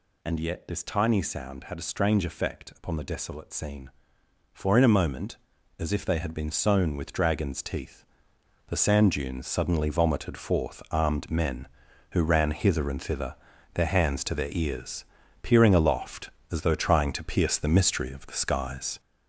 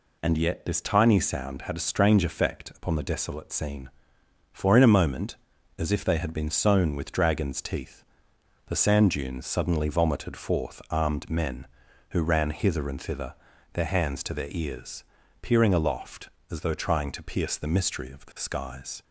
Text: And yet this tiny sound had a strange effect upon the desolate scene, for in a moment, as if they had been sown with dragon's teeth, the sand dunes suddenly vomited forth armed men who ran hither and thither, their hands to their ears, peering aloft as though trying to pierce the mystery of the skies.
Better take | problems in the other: second | gets louder; noticeable; throughout; 6 dB

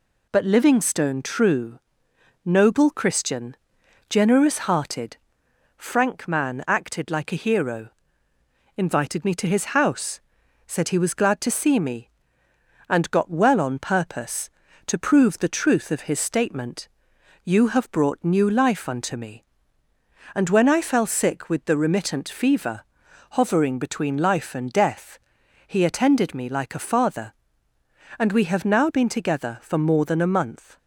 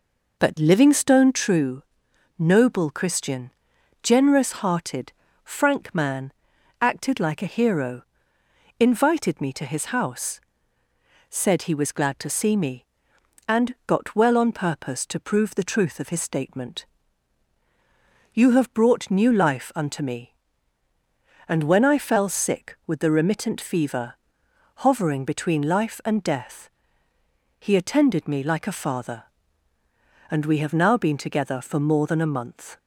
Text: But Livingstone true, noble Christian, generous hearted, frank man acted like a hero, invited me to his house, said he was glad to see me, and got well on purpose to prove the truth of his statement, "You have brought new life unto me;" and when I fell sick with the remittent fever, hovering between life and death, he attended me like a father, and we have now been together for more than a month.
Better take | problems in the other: first | starts louder than the rest; noticeable; until 1.5 s; 5 dB // pauses between "man" and "acted"; noticeable; at 6.3 s; 0.48 s long

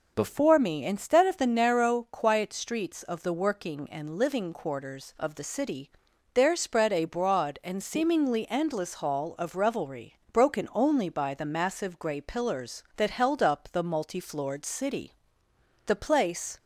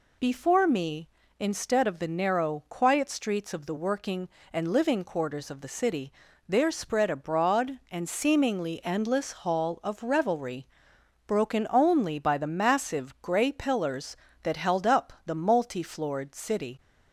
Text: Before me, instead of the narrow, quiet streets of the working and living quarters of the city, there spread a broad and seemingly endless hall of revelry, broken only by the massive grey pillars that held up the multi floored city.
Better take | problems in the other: second | goes on to say "The place"; noticeable; from 15.8 s on; 0.72 s long

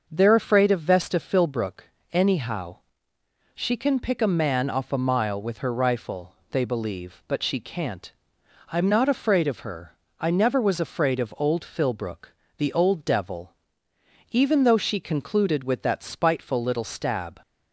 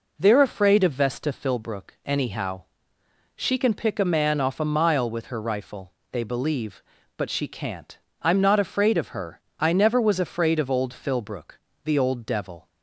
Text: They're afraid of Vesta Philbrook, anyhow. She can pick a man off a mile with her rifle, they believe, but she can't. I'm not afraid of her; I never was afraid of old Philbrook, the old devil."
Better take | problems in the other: second | starts louder than the rest; noticeable; until 1.1 s; 6 dB // goes on to say "Even though she concluded with that spiteful little stab"; strong; from 14.3 s on; 3.1 s long

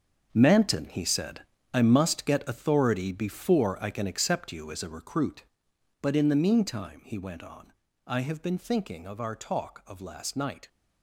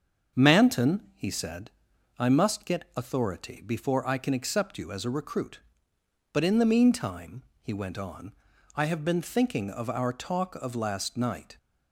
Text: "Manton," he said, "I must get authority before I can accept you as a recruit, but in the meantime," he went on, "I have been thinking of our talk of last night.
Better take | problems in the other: second | gets quieter; strong; throughout; 11.5 dB // starts louder than the rest; until 1.3 s; 6.5 dB; also in the second

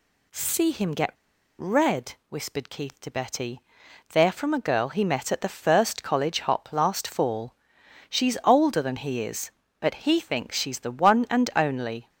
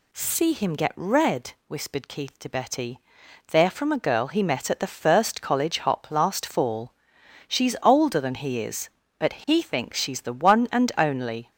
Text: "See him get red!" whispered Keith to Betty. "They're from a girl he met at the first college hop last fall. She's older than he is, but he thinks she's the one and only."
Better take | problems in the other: second | pauses between "get" and "red"; noticeable; at 1.0 s; 0.49 s long

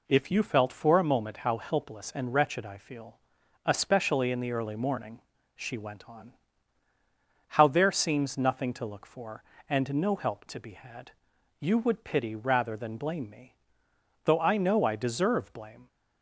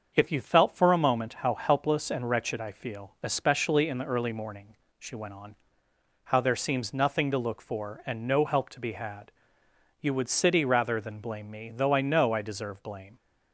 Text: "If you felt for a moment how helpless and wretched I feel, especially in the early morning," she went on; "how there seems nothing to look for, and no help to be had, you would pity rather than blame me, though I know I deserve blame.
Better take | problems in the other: first | starts louder than the rest; until 1.1 s; 6.5 dB // says "city" for "pity"; at 10.2 s

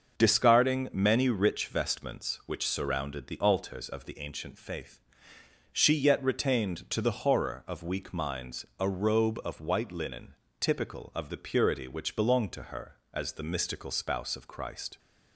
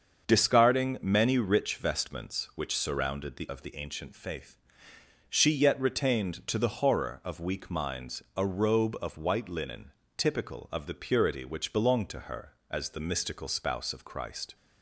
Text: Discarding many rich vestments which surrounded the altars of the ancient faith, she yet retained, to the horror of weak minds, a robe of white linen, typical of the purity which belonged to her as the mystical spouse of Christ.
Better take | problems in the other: first | starts louder than the rest; until 1.3 s; 6.5 dB; also in the first // skips "altars"; at 3.4 s

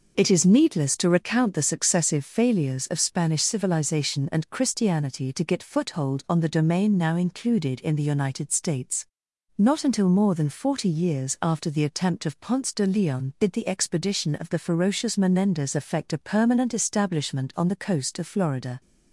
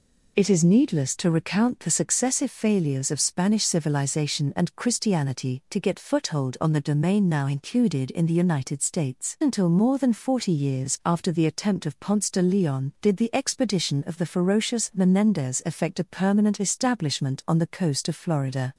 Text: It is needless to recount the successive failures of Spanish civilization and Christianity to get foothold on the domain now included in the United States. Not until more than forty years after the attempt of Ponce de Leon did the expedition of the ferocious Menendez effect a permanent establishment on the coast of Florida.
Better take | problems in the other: first | skips "Not"; at 9.3 s

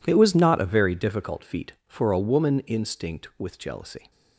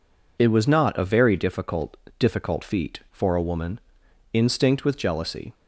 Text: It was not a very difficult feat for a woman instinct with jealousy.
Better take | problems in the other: first | says "difficult" twice; at 2.1 s // pauses between "woman" and "instinct"; noticeable; at 3.7 s; 0.52 s long

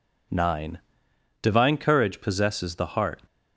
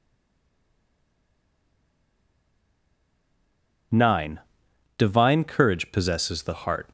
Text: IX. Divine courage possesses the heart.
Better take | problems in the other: first | stays silent before the first word; strong; until 3.9 s; 3.9 s long

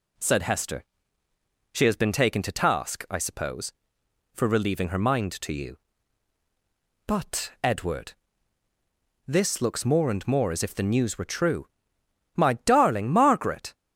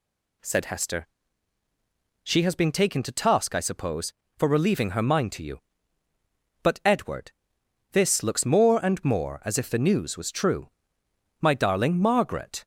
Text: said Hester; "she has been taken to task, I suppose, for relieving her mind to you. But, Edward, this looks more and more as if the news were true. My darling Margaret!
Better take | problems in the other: first | says "was" for "were"; at 10.1 s

